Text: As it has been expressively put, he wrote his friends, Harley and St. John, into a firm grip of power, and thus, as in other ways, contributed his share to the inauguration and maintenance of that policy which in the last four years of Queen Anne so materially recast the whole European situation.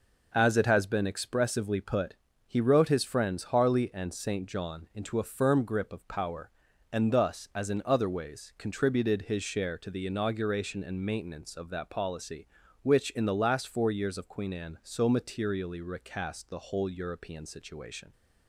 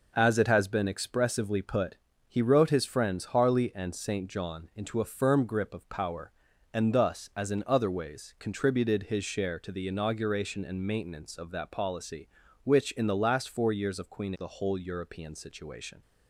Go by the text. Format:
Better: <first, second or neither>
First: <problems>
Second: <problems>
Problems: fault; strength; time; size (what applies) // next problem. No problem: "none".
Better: first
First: none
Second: skips "Anne so materially recast"; at 14.3 s